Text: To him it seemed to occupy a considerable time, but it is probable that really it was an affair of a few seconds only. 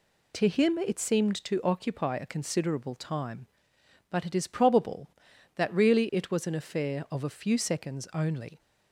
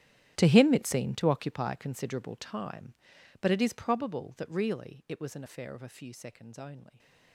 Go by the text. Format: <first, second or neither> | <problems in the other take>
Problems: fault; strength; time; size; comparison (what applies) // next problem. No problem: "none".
first | gets quieter; strong; throughout; 17.5 dB